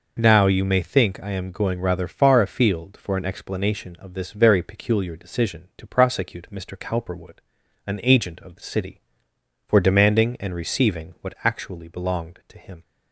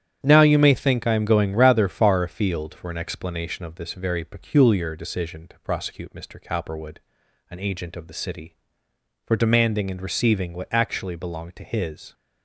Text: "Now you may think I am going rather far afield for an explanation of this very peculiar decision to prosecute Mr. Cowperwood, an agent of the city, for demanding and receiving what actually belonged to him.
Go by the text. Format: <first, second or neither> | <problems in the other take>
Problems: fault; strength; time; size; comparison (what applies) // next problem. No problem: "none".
first | starts louder than the rest; strong; until 1.2 s; 10 dB // says "his" for "him"; at 11.6 s